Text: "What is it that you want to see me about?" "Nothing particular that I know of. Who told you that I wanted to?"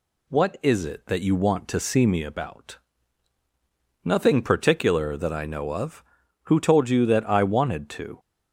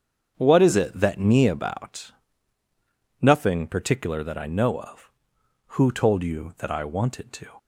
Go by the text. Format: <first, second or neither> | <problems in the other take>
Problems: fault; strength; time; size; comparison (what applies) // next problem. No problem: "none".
first | starts louder than the rest; until 1.3 s; 7 dB // skips "you want to see"; at 1.1 s